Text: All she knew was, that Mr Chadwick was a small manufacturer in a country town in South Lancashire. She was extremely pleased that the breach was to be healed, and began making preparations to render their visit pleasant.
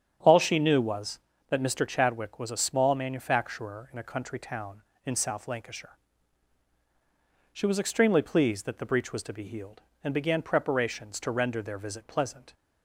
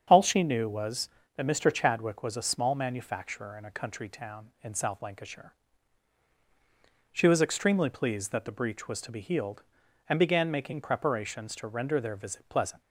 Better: second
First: starts louder than the rest; strong; until 1.5 s; 8.5 dB // skips "making"; at 10.4 s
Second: starts louder than the rest; strong; until 1.0 s; 7.5 dB

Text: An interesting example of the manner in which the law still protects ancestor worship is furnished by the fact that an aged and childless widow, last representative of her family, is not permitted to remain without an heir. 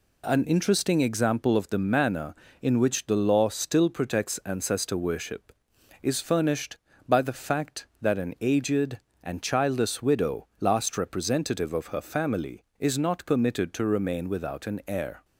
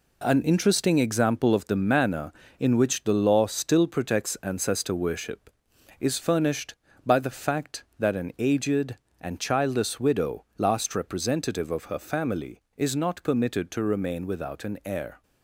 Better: first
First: none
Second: gets quieter; throughout; 7 dB

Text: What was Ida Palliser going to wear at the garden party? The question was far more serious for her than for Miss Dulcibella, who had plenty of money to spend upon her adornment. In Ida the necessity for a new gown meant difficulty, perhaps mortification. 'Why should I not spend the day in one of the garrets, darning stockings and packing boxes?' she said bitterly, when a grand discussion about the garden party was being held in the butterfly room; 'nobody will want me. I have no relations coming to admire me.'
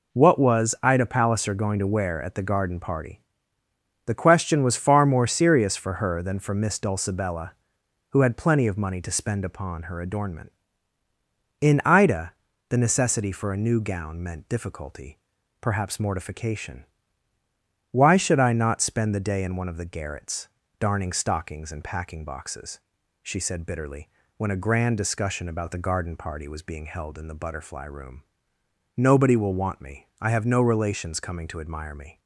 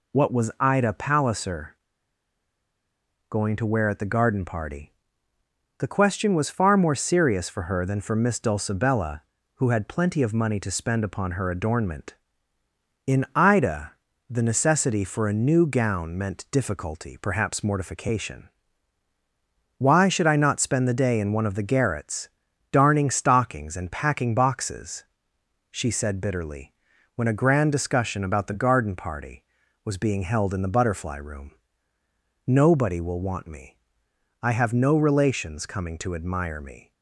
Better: first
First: pauses between "Ida" and "the"; slight; at 12.3 s; 0.36 s long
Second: pauses between "Palliser" and "going"; strong; at 1.7 s; 1.5 s long // pauses between "Ida" and "the"; at 13.9 s; 0.40 s long

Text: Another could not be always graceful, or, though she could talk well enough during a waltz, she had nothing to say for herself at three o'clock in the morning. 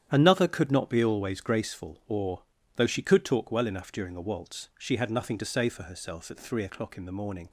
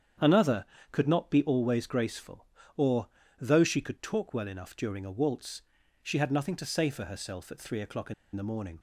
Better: first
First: starts louder than the rest; strong; until 1.1 s; 9.5 dB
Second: starts louder than the rest; strong; until 1.4 s; 8.5 dB // pauses between "in" and "the"; slight; at 8.1 s; 0.21 s long

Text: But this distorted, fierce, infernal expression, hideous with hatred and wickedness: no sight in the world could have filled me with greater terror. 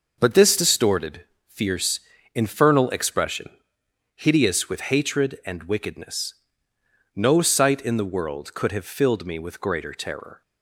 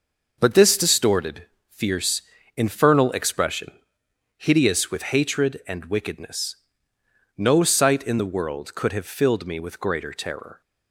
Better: neither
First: none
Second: none

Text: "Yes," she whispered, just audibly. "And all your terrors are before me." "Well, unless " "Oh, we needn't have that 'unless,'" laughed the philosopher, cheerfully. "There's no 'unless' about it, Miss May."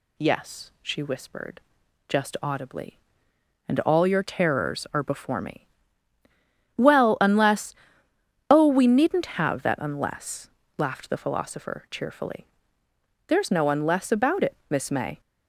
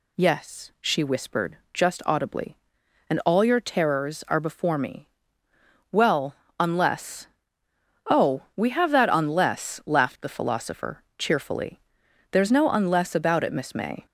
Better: first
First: none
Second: skips "needn't"; at 8.6 s

